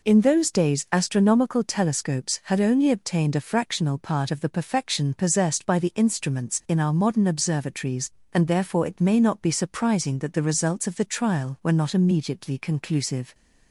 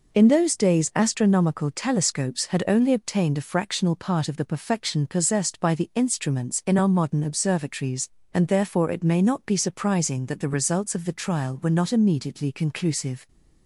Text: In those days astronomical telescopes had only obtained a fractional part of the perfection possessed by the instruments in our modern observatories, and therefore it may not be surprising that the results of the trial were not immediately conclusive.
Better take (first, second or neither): neither